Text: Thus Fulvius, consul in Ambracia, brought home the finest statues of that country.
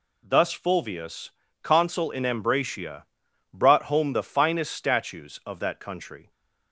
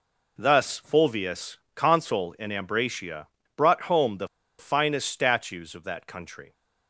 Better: first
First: none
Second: pauses between "the" and "finest"; slight; at 4.2 s; 0.31 s long

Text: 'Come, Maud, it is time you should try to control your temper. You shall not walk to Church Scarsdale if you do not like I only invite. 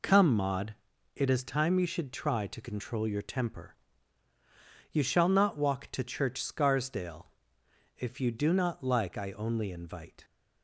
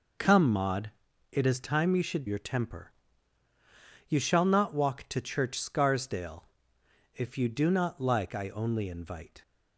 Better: first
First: pauses between "Scarsdale" and "if"; noticeable; at 7.2 s; 0.70 s long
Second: skips "try to control"; at 2.2 s // pauses between "Scarsdale" and "if"; noticeable; at 6.4 s; 0.70 s long

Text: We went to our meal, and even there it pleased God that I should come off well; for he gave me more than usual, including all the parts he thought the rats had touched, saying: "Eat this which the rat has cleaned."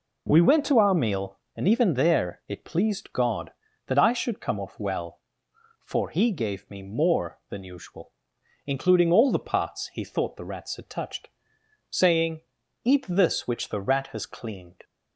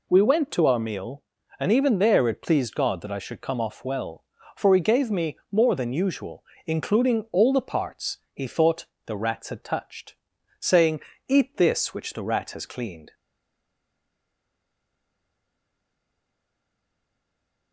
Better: first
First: none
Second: pauses between "thought" and "the"; slight; at 8.8 s; 0.20 s long // stays silent after the last word; strong; from 13.1 s on; 4.6 s long

